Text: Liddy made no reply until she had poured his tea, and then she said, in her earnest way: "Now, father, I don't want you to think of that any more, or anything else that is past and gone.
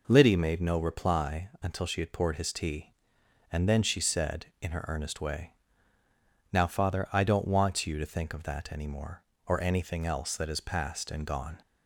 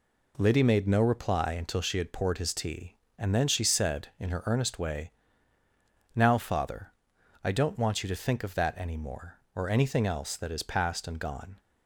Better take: neither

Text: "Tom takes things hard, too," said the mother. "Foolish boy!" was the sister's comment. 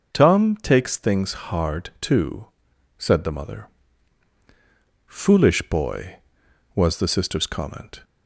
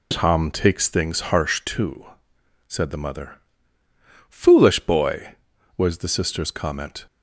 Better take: first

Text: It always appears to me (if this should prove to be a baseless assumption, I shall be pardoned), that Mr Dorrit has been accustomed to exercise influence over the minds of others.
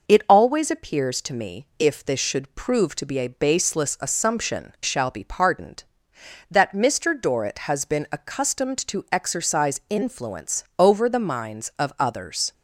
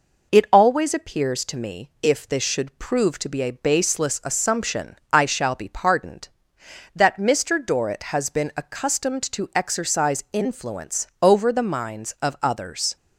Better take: second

